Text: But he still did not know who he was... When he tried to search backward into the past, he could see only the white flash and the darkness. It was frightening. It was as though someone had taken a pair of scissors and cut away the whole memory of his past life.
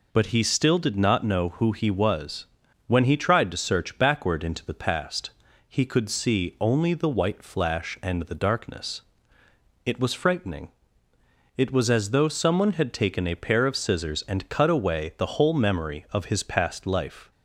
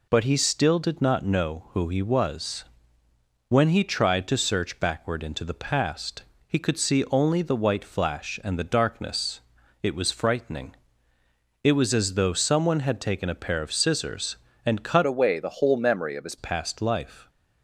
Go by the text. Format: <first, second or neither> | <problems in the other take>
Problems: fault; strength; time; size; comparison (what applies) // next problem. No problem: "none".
first | changes voice from "away" to "his"; from 15.0 to 16.3 s; 1.3 s long